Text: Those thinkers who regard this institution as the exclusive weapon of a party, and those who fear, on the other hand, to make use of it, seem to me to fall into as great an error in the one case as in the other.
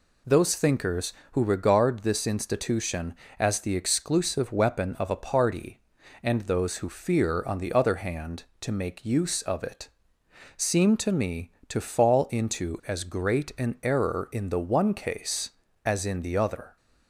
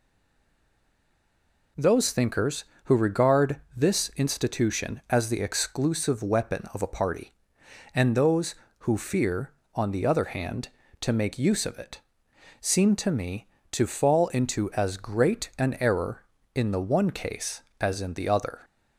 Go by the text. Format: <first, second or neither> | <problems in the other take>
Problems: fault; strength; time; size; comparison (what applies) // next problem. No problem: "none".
first | stays silent before the first word; noticeable; until 1.7 s; 1.7 s long // pauses between "regard" and "this"; slight; at 3.6 s; 0.16 s long